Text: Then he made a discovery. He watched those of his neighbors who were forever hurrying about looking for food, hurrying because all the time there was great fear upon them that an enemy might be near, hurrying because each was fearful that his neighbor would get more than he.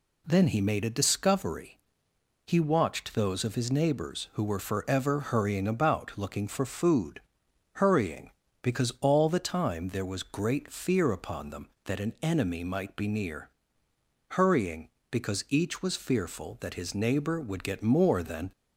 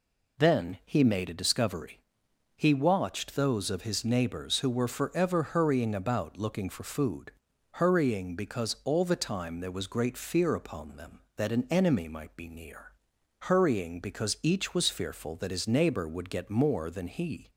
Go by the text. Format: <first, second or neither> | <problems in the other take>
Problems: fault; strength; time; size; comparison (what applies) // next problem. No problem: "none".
second | stops before "he"; at 18.5 s